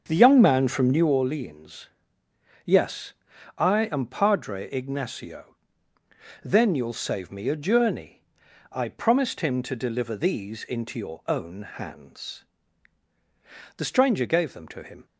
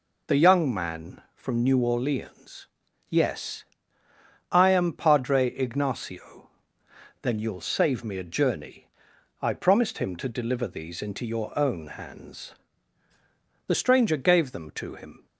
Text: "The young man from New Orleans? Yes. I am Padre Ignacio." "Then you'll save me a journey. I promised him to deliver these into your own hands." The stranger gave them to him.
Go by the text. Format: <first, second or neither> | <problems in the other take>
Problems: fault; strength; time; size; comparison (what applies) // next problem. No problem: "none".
second | starts louder than the rest; until 1.2 s; 7 dB